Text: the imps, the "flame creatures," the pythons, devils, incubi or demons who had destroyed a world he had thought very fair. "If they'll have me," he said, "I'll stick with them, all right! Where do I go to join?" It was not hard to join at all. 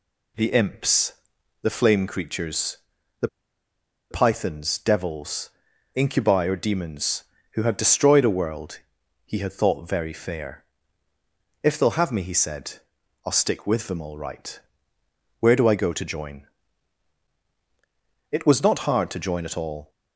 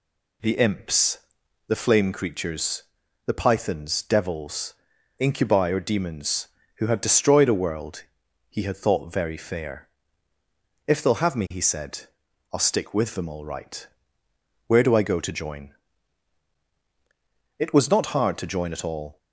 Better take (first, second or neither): second